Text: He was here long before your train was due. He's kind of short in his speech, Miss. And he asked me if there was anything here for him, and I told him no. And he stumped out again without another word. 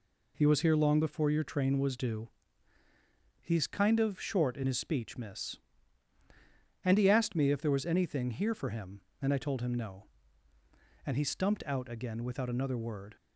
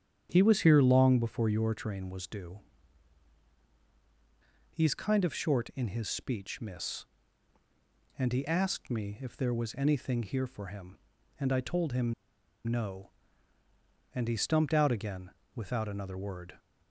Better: first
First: none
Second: starts louder than the rest; strong; until 1.3 s; 9 dB // pauses between "him" and "no"; noticeable; at 12.1 s; 0.51 s long // pauses between "again" and "without"; slight; at 15.2 s; 0.24 s long

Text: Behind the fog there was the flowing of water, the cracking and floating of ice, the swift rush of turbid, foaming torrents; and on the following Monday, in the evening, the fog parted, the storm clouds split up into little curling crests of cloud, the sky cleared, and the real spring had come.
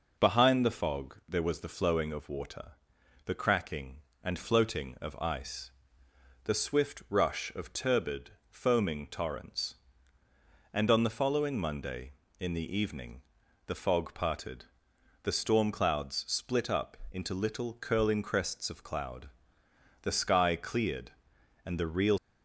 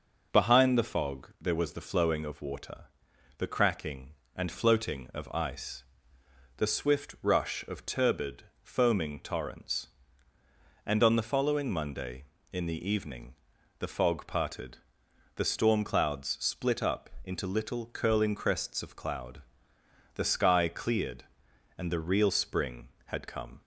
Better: second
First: pauses between "up" and "into"; slight; at 16.9 s; 0.16 s long // stops before "spring had come"; at 22.1 s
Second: pauses between "up" and "into"; slight; at 17.0 s; 0.16 s long

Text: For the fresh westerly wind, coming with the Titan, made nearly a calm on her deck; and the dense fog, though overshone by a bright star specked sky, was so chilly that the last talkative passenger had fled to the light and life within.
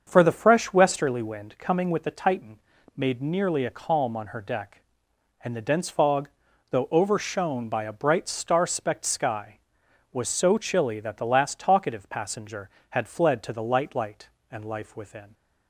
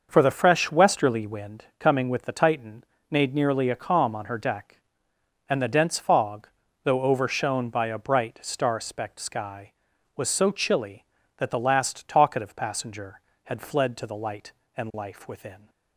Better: second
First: starts louder than the rest; until 1.0 s; 7 dB // says "light" twice; at 13.9 s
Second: starts louder than the rest; until 1.1 s; 6 dB

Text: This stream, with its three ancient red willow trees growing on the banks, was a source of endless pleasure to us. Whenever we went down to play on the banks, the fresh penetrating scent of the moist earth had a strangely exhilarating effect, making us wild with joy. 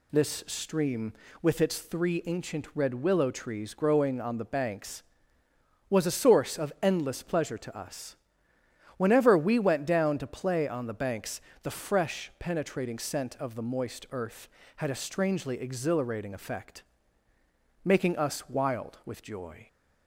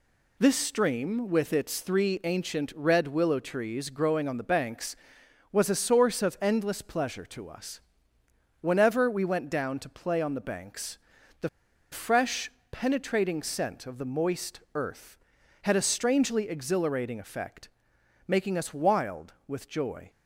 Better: first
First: none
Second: pauses between "the" and "fresh"; at 11.4 s; 0.42 s long // pauses between "fresh" and "penetrating"; slight; at 12.4 s; 0.22 s long

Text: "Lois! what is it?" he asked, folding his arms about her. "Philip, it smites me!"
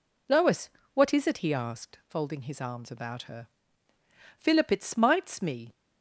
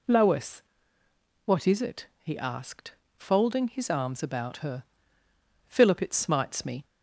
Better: neither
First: none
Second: none

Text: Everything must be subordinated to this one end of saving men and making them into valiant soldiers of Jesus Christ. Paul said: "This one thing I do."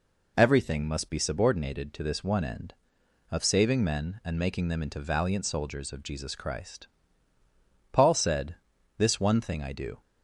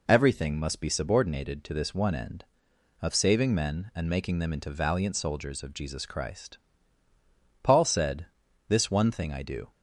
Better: neither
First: none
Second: none

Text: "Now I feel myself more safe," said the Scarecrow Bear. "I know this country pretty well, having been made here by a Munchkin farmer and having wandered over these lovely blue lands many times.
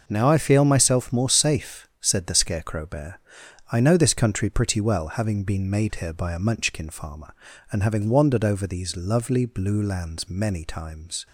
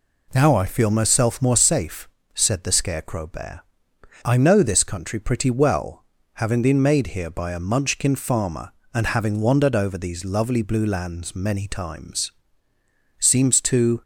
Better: first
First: none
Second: goes on to say "Seems to"; noticeable; from 13.1 s on; 0.82 s long

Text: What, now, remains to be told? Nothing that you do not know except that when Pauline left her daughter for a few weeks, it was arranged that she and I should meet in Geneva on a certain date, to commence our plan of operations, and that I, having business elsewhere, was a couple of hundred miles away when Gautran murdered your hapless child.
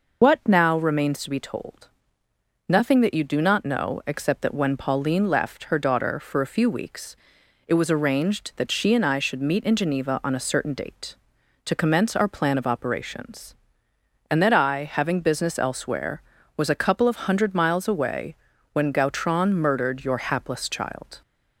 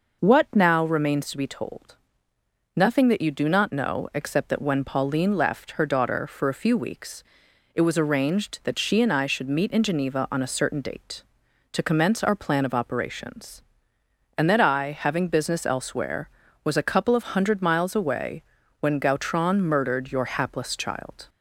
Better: second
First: loses the start of "What"; at 0.2 s; 80 ms // pauses between "away" and "when"; at 18.3 s; 0.38 s long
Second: pauses between "away" and "when"; at 18.4 s; 0.38 s long

